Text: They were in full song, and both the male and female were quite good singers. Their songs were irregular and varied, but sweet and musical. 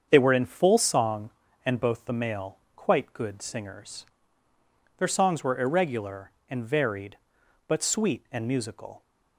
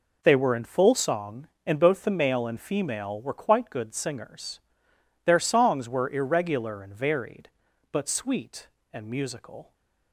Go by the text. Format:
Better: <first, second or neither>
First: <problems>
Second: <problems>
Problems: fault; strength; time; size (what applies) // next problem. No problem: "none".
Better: second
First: starts louder than the rest; strong; until 1.1 s; 7 dB // skips "and female were"; at 2.6 s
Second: none